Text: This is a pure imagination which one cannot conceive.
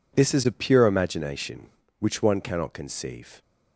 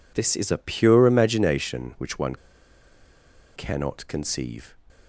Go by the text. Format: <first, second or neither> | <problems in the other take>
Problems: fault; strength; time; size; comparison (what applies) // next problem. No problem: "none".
first | pauses between "one" and "cannot"; at 2.3 s; 1.2 s long